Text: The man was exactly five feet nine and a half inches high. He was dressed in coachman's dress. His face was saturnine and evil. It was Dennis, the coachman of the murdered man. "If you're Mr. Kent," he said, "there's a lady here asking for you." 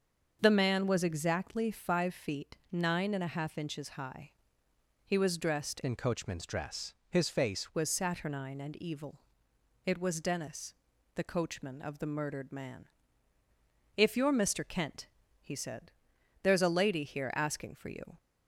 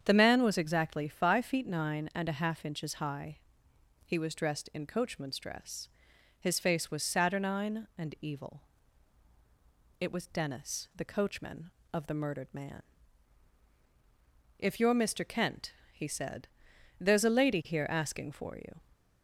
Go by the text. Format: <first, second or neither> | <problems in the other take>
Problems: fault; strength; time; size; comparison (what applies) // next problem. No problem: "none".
second | starts louder than the rest; until 1.4 s; 7 dB; strong in the second // pauses between "feet" and "nine"; slight; at 2.5 s; 0.16 s long // changes voice from "in" to "face"; from 5.8 to 7.7 s; 1.9 s long